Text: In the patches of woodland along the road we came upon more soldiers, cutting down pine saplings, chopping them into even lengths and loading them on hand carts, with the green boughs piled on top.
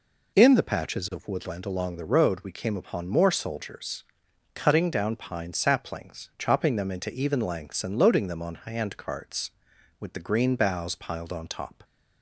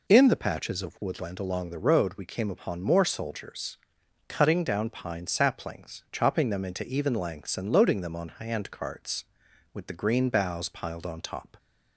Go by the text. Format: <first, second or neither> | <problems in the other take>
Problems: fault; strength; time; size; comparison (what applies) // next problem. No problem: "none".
neither | none